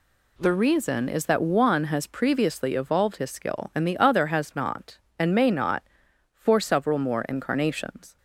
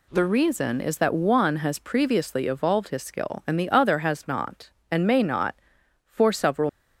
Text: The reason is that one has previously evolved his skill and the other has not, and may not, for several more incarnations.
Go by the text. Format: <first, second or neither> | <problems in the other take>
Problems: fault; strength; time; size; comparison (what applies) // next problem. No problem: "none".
first | stops before "more incarnations"; at 6.6 s